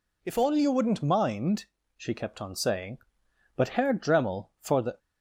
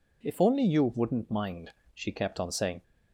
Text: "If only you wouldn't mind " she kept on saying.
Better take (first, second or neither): second